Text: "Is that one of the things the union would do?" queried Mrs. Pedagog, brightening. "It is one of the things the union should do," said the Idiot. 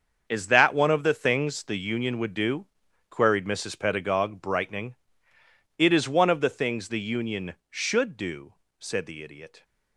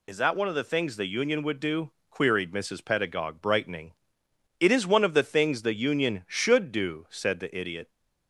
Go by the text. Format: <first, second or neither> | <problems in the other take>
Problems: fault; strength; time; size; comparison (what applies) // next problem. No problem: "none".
second | gets quieter; strong; throughout; 11 dB